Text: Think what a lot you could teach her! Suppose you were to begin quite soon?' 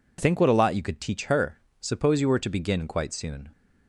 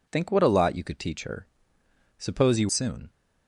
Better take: first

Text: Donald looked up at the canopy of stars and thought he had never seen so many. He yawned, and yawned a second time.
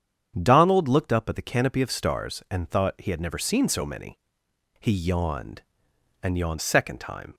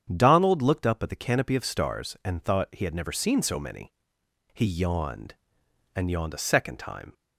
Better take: second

